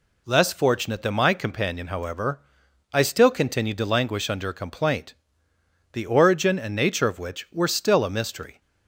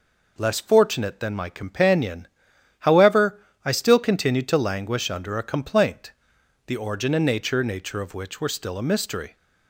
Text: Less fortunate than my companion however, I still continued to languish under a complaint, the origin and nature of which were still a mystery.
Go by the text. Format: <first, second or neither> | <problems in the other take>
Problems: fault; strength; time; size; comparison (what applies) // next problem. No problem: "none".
first | pauses between "companion" and "however"; noticeable; at 2.2 s; 0.52 s long // says "nature" twice; at 7.6 s